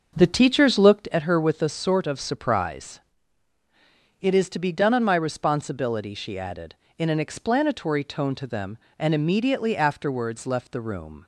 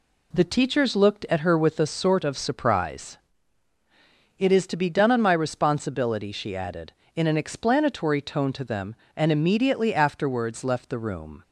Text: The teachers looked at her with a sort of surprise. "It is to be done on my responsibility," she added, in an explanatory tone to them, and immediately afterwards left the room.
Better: second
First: starts louder than the rest; until 1.0 s; 6 dB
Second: none

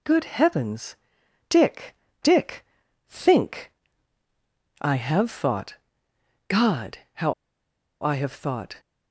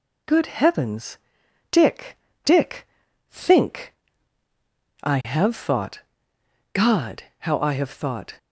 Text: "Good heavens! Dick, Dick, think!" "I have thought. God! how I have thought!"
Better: second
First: pauses between "how" and "I"; noticeable; at 7.3 s; 0.69 s long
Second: none

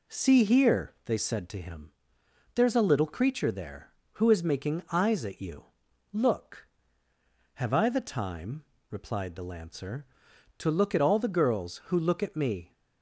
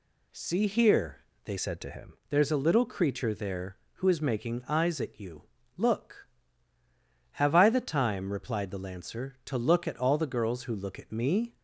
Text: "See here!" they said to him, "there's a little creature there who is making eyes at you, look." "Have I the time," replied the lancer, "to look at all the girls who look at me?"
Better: first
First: none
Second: changes voice from "said" to "him"; from 1.5 to 2.1 s; 0.6 s long

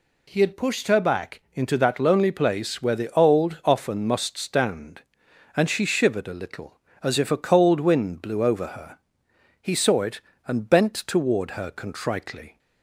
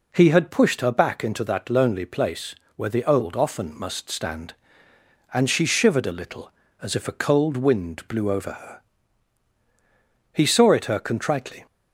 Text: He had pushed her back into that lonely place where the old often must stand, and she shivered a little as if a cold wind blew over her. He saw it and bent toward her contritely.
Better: first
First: none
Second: pauses between "place" and "where"; slight; at 2.5 s; 0.20 s long // skips "and bent toward"; at 10.8 s

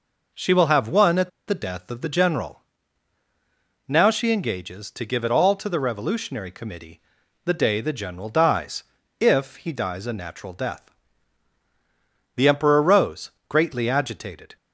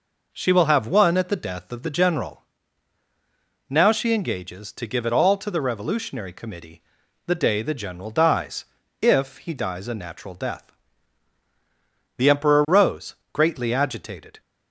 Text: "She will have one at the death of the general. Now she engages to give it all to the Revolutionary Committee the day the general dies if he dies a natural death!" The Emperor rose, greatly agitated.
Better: second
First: pauses between "at" and "the"; slight; at 1.2 s; 0.19 s long // pauses between "Committee" and "the"; at 6.9 s; 0.44 s long // pauses between "dies" and "if"; slight; at 8.8 s; 0.36 s long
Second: pauses between "Committee" and "the"; at 6.8 s; 0.44 s long // pauses between "dies" and "if"; slight; at 8.6 s; 0.36 s long

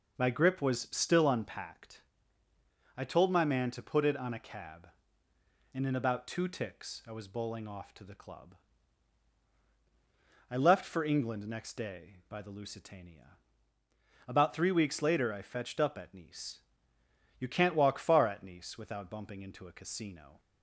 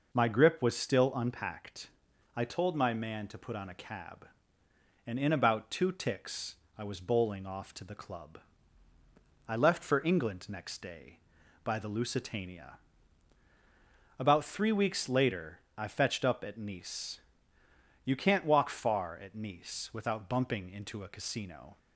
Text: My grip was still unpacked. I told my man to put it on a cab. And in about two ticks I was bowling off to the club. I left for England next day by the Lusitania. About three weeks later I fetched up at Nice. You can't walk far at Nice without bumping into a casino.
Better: first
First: none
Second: skips "it"; at 3.5 s // pauses between "ticks" and "I"; slight; at 6.5 s; 0.22 s long // pauses between "later" and "I"; slight; at 15.5 s; 0.16 s long

